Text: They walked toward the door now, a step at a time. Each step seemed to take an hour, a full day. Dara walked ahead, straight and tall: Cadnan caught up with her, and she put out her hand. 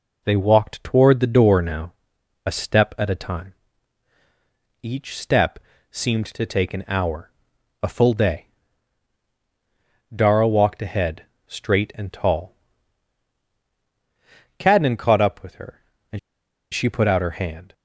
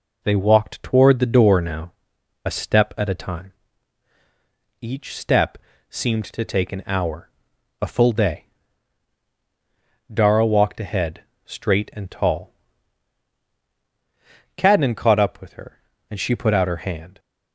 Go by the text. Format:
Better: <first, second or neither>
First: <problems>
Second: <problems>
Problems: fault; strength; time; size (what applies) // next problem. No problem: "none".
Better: second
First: pauses between "step" and "seemed"; slight; at 5.5 s; 0.32 s long // pauses between "and" and "she"; noticeable; at 16.1 s; 0.53 s long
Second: pauses between "step" and "seemed"; slight; at 5.5 s; 0.32 s long